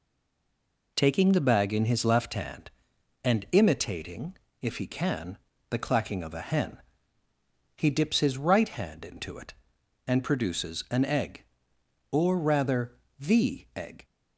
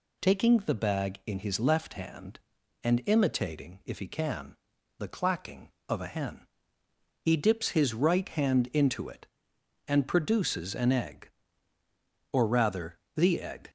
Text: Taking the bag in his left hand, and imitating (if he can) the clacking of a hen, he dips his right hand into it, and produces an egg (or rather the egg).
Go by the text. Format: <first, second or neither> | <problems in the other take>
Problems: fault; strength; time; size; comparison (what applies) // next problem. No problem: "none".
second | stays silent before the first word; slight; until 0.9 s; 0.9 s long // pauses between "rather" and "the"; slight; at 12.9 s; 0.28 s long; slight in the second